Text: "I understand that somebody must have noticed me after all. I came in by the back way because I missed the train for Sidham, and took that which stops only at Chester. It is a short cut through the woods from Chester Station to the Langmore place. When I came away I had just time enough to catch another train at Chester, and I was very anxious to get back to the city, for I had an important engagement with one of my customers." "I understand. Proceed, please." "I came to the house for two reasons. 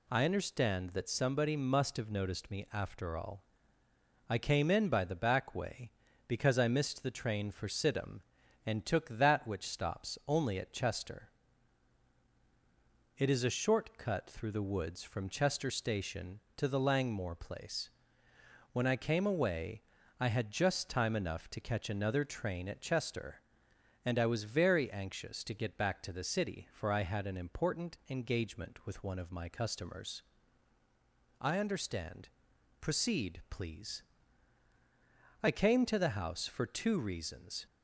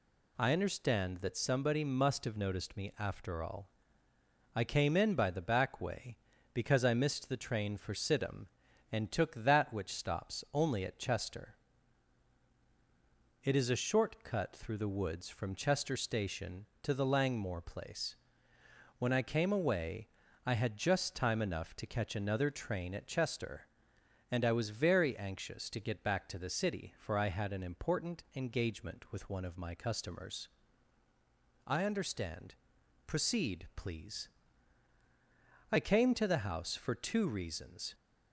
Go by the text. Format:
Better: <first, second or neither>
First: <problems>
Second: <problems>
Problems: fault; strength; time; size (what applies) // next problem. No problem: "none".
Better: neither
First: pauses between "away" and "I"; slight; at 19.8 s; 0.36 s long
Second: pauses between "away" and "I"; slight; at 20.0 s; 0.36 s long